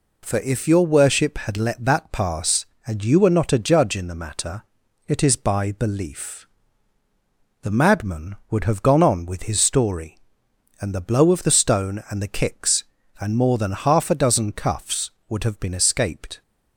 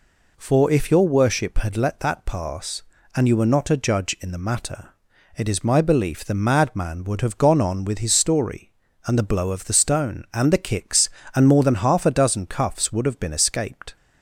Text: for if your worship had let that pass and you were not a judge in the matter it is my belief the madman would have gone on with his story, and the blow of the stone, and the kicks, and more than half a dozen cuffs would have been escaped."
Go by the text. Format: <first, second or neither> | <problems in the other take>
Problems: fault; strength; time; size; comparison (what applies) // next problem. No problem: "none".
second | pauses between "matter" and "it"; at 4.6 s; 0.42 s long; noticeable in the second // says "by" for "my"; at 5.3 s // pauses between "belief" and "the"; at 6.4 s; 1.1 s long